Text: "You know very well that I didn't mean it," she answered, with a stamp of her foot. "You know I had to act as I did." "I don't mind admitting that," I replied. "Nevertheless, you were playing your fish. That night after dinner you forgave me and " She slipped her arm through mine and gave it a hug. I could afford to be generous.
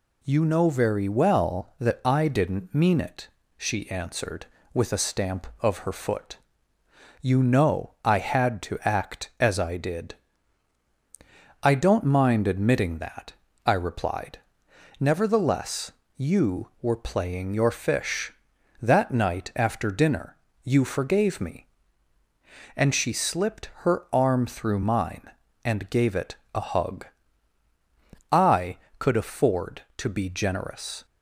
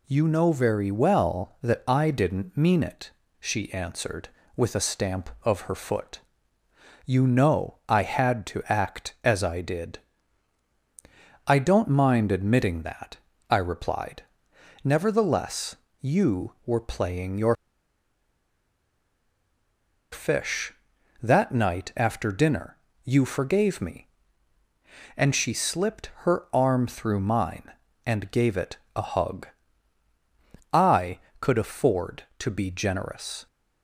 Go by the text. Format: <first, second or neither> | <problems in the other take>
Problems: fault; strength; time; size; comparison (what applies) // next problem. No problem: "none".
first | pauses between "your" and "fish"; strong; at 17.5 s; 2.5 s long // pauses between "dinner" and "you"; slight; at 22.7 s; 0.28 s long; slight in the first // pauses between "it" and "a"; slight; at 28.7 s; 0.18 s long; slight in the first